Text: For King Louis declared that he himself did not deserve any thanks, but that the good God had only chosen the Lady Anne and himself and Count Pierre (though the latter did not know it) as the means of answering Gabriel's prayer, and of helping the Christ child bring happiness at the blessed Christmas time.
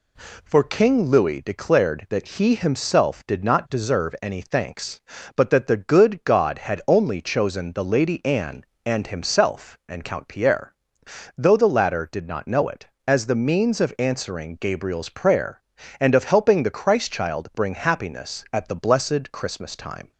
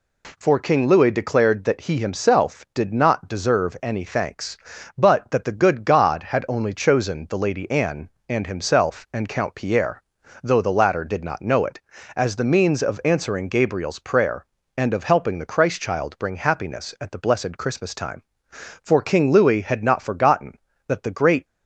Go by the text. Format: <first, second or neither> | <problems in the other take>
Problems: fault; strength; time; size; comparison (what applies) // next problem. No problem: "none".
first | goes on to say "For King Louis had not forgotten that the great"; strong; from 18.4 s on; 2.9 s long